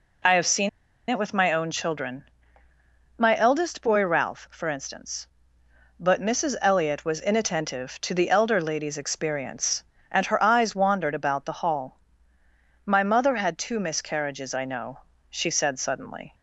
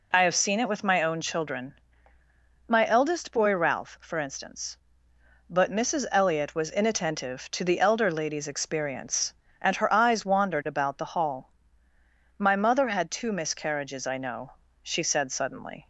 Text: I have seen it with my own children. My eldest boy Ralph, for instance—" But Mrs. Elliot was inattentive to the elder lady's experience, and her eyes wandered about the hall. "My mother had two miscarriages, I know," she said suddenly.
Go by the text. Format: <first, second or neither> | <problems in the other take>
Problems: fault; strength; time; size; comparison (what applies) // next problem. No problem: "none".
second | pauses between "seen" and "it"; at 0.6 s; 0.41 s long